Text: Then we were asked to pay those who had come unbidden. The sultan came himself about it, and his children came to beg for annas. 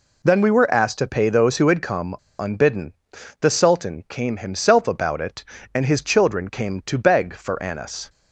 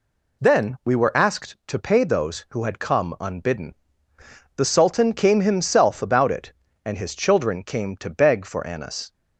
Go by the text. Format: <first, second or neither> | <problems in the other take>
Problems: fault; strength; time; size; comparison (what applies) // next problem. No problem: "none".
second | pauses between "come" and "unbidden"; slight; at 2.1 s; 0.24 s long